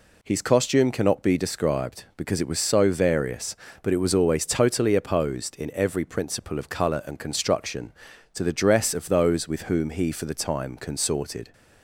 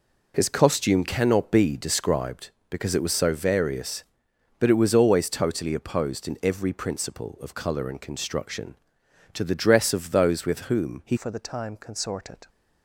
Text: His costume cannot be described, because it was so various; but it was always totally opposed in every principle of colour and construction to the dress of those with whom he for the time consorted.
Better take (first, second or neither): first